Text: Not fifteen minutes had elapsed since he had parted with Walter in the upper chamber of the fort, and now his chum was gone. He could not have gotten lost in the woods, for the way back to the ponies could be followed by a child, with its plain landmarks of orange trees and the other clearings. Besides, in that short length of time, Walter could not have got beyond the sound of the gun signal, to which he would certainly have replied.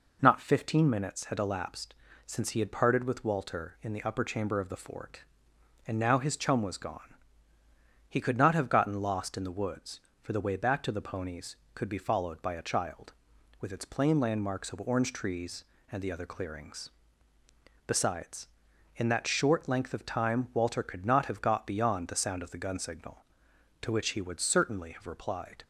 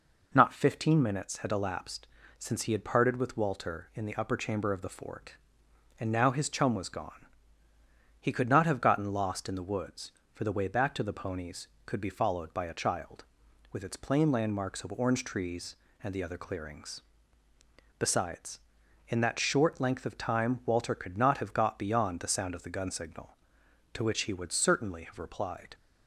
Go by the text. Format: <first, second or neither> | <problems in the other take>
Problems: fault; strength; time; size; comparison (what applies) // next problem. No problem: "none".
neither | pauses between "elapsed" and "since"; slight; the same in both